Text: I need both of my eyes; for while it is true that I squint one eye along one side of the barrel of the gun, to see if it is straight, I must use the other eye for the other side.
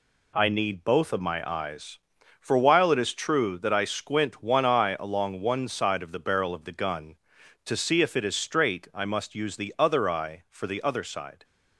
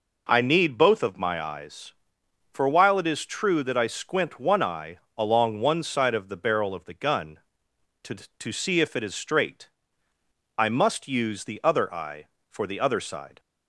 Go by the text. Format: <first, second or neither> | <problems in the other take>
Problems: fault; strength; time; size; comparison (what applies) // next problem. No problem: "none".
first | pauses between "eye" and "along"; slight; at 4.9 s; 0.20 s long // says "to" twice; at 8.3 s